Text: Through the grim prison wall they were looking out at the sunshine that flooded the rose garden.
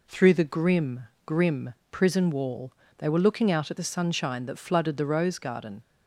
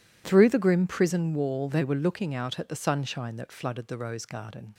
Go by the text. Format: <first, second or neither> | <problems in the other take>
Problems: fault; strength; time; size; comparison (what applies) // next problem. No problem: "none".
second | says "grim" twice; at 1.2 s // pauses between "wall" and "they"; slight; at 2.7 s; 0.26 s long